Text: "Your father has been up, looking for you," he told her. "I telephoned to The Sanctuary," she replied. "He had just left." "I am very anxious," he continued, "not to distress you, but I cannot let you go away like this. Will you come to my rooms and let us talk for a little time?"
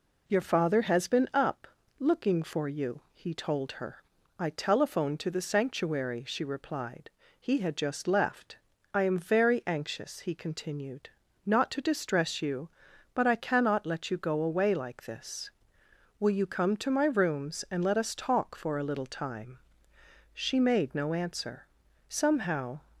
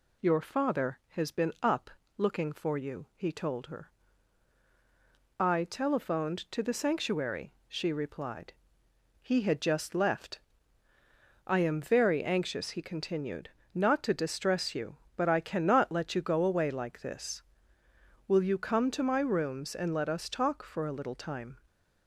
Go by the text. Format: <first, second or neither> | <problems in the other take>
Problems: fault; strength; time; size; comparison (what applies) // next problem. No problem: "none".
second | goes on to say "She made no answer Somehow"; strong; from 20.3 s on; 2.4 s long